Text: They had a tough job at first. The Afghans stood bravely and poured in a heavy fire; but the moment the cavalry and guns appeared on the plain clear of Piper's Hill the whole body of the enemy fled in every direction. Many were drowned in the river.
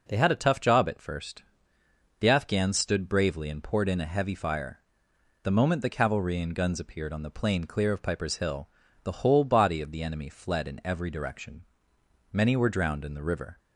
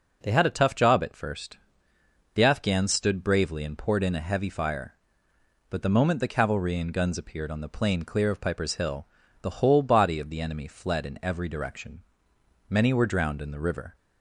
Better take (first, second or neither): second